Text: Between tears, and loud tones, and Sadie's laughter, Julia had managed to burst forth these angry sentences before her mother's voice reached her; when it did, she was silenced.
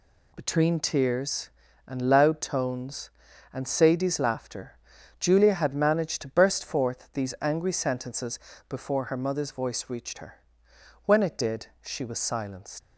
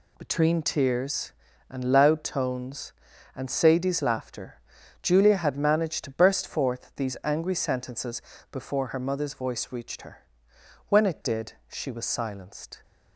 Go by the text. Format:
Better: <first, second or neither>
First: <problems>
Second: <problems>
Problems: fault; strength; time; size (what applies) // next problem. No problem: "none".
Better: second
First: pauses between "sentences" and "before"; slight; at 8.3 s; 0.28 s long // leaves "silenced" unfinished; at 12.8 s; 150 ms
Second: pauses between "sentences" and "before"; slight; at 8.2 s; 0.28 s long